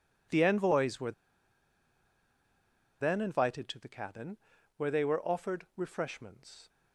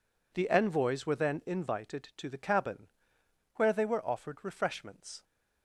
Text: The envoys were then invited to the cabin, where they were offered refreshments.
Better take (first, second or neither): second